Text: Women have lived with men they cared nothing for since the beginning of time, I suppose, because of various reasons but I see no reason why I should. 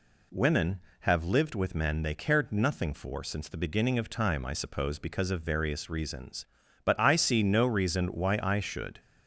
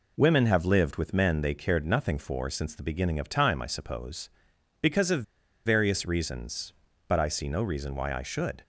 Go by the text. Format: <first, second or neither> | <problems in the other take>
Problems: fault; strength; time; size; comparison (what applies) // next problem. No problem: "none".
first | pauses between "of" and "various"; at 5.2 s; 0.42 s long